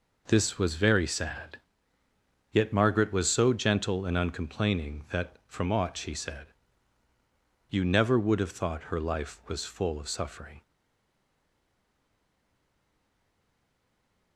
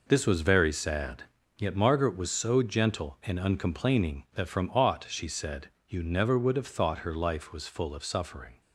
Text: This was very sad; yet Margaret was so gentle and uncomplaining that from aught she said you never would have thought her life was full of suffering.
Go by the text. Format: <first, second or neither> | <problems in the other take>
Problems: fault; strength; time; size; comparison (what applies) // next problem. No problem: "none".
second | pauses between "said" and "you"; at 6.4 s; 1.2 s long; slight in the second // stays silent after the last word; strong; from 10.6 s on; 3.7 s long